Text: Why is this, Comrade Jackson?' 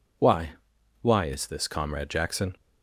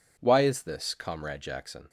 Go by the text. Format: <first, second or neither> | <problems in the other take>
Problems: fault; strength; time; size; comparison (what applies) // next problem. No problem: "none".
second | says "Why" twice; at 1.0 s